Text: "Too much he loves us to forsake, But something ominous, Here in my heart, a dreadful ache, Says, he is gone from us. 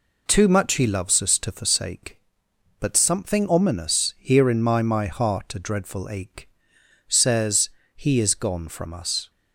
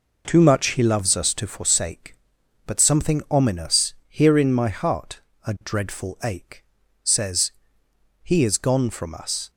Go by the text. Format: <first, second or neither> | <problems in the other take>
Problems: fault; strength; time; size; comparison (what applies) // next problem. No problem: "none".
second | says "my" twice; at 4.7 s